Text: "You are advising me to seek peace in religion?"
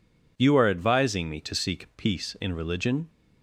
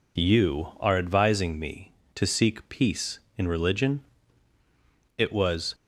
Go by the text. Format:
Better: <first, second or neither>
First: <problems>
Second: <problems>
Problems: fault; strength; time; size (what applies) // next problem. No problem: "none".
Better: first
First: none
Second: goes on to say "It was"; from 5.1 s on; 0.56 s long